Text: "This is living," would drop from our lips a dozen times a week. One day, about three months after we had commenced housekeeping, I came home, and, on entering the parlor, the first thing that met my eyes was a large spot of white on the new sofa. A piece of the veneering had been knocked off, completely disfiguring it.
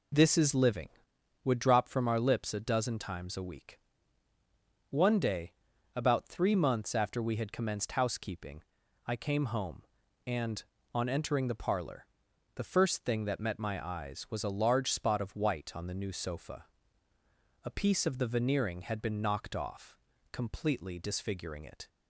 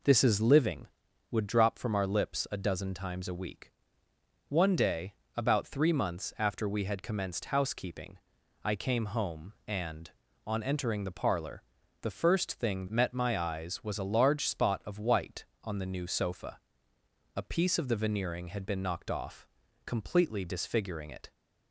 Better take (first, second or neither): first